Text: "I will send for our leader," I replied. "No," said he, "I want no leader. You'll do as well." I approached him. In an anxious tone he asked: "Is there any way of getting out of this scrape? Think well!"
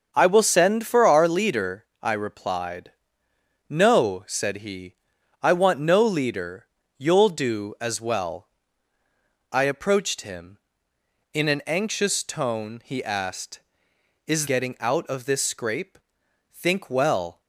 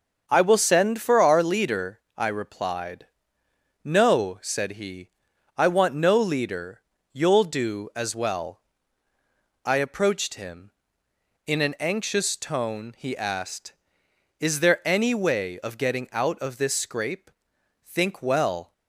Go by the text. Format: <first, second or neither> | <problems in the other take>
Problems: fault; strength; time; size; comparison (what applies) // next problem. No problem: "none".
second | starts louder than the rest; until 1.1 s; 6.5 dB; also in the second // skips "there any way of"; at 14.4 s